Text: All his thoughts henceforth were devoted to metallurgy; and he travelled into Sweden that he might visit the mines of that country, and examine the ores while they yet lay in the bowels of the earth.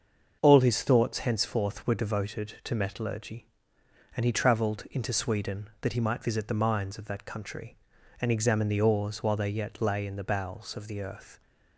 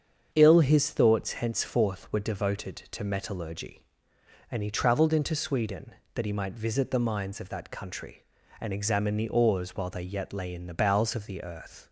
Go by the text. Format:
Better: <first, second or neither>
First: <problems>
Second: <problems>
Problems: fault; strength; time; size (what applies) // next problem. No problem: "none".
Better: first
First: starts louder than the rest; until 1.4 s; 6.5 dB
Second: starts louder than the rest; strong; until 1.3 s; 7.5 dB // says "Ill" for "All"; at 0.3 s